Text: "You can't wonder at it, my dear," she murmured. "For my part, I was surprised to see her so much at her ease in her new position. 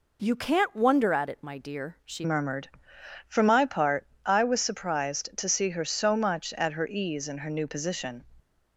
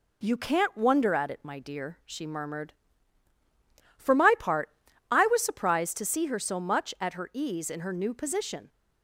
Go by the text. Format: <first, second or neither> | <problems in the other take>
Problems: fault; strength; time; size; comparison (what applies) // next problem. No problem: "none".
second | changes voice at "murmured"; from 2.2 s on; 6.0 s long